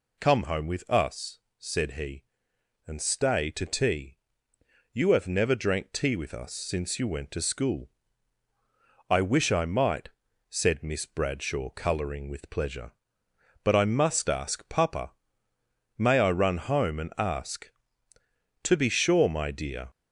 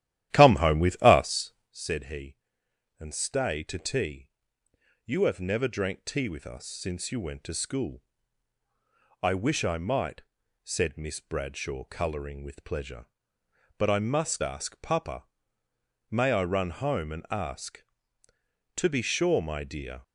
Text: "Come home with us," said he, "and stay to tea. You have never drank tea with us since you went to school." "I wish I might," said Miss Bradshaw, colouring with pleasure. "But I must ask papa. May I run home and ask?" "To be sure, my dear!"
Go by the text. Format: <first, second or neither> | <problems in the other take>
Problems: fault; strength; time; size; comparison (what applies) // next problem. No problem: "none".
first | starts louder than the rest; strong; until 1.8 s; 12.5 dB